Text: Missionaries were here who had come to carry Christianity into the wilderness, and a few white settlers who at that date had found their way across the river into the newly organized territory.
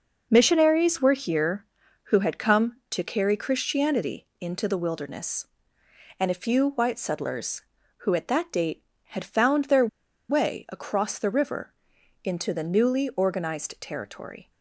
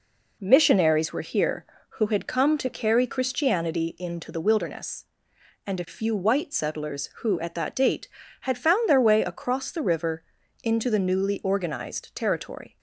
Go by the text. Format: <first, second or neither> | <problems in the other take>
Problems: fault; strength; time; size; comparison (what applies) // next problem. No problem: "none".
second | pauses between "their" and "way"; at 9.8 s; 0.42 s long // pauses between "river" and "into"; noticeable; at 11.7 s; 0.50 s long; also in the second